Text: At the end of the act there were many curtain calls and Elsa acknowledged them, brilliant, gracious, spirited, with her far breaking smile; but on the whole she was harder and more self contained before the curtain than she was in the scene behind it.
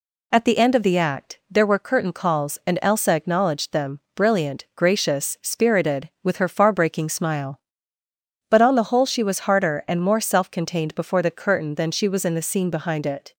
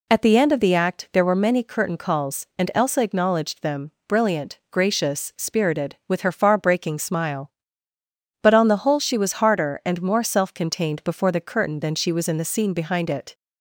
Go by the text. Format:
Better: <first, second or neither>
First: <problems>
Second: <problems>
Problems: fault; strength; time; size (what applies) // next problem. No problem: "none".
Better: second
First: skips "many"; at 1.7 s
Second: none